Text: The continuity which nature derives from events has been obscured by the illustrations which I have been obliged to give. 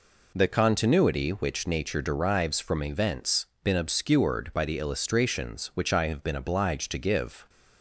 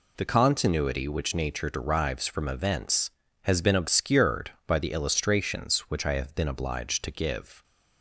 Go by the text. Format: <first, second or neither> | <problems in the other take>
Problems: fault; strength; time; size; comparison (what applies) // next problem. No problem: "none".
second | skips "has"; at 3.5 s